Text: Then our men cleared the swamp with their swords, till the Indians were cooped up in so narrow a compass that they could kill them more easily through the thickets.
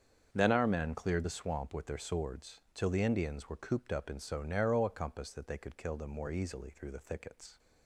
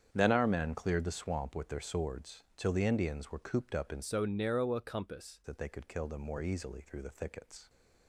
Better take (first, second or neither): first